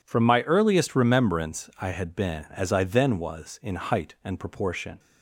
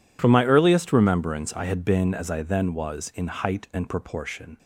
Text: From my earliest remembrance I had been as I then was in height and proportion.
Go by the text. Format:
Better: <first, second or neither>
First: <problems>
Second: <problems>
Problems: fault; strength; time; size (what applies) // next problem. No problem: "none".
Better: neither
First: none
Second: none